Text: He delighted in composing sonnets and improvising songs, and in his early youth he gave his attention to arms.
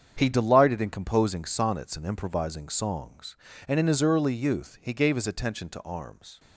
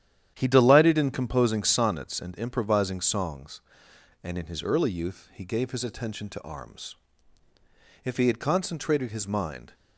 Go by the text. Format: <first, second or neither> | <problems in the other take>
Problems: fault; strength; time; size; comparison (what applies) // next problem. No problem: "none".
first | starts louder than the rest; strong; until 1.3 s; 10.5 dB; strong in the first // goes on to say "If he had concentrated his mind"; strong; from 8.0 s on; 1.7 s long